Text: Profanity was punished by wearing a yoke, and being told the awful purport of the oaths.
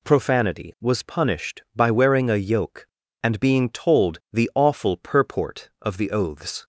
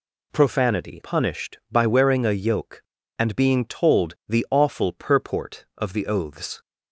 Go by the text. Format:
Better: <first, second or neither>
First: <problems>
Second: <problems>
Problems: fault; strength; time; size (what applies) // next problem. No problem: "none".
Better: first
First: none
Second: skips "was"; at 1.0 s